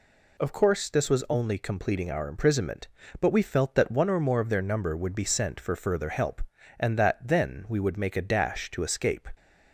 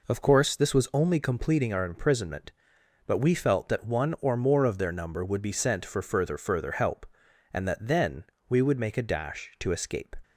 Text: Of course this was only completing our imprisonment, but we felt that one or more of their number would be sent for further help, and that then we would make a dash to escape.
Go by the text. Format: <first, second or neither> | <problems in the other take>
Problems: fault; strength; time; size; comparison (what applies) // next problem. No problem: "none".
first | says "further" twice; at 6.3 s // pauses between "then" and "we"; slight; at 8.2 s; 0.24 s long